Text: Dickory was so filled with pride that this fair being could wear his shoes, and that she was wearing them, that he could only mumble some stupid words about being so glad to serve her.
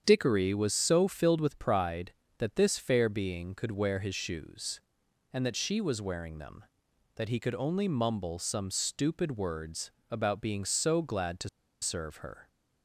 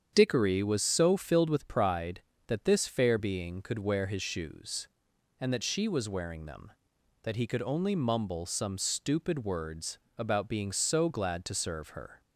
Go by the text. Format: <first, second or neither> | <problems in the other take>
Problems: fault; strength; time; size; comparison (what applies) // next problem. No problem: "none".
second | starts louder than the rest; strong; until 1.0 s; 8 dB; strong in the second // pauses between "words" and "about"; slight; at 9.8 s; 0.22 s long; slight in the second // pauses between "to" and "serve"; slight; at 11.4 s; 0.32 s long